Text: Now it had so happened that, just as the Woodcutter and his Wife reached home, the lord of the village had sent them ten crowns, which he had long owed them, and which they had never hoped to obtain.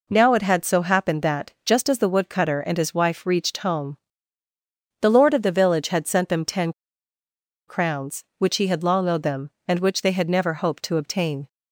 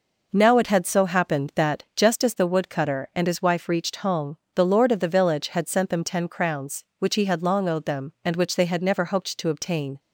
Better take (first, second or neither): second